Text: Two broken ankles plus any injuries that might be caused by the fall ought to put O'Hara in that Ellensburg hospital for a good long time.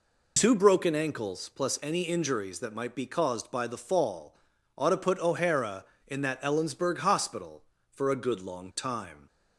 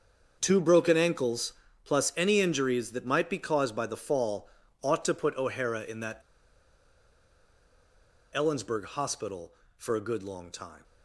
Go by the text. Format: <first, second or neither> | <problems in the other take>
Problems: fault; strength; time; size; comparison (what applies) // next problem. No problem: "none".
first | starts louder than the rest; until 1.4 s; 6.5 dB // pauses between "ankles" and "plus"; slight; at 1.5 s; 0.32 s long // pauses between "fall" and "ought"; slight; at 4.4 s; 0.34 s long; also in the first // pauses between "that" and "Ellensburg"; strong; at 6.2 s; 2.1 s long